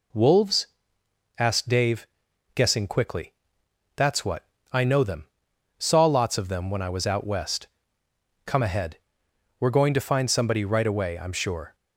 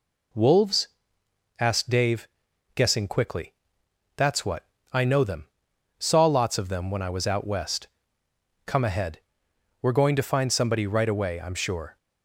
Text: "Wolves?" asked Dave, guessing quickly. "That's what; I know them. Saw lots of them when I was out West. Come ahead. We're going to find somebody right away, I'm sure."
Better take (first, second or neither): neither